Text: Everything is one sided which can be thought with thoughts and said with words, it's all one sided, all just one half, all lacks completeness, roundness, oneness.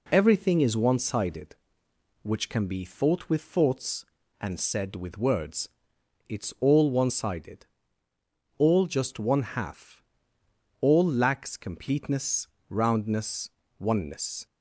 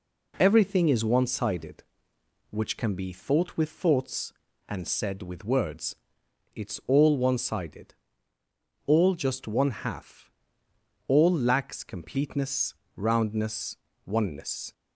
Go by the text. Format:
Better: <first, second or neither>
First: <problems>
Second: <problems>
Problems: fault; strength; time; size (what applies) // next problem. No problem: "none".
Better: neither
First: none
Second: none